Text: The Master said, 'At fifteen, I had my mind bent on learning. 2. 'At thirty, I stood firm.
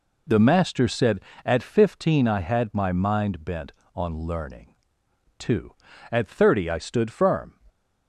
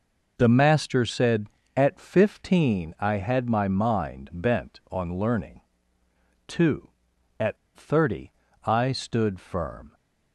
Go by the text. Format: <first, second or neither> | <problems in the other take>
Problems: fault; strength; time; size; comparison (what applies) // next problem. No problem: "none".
first | pauses between "At" and "thirty"; slight; at 7.5 s; 0.19 s long